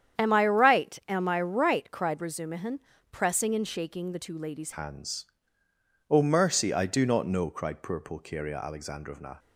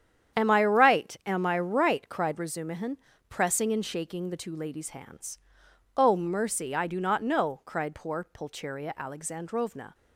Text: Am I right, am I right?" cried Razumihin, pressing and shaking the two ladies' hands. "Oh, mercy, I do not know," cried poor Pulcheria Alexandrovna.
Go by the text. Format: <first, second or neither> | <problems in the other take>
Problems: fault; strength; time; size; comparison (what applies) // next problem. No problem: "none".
second | starts louder than the rest; strong; until 1.3 s; 9 dB; strong in the second // changes voice at "hands"; from 4.7 s on; 4.6 s long